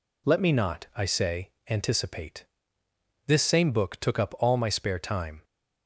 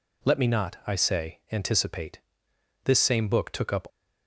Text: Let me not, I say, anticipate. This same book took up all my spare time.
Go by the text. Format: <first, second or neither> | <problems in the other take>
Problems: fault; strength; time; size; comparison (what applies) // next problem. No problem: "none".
first | stops before "all my spare time"; at 3.8 s